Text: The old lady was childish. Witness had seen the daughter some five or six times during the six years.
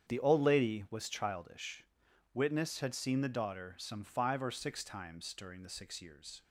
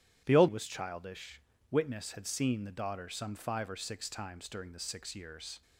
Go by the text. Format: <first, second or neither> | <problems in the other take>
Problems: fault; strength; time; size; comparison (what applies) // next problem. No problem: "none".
first | starts louder than the rest; strong; until 1.2 s; 11 dB; strong in the first // skips "lady"; at 0.4 s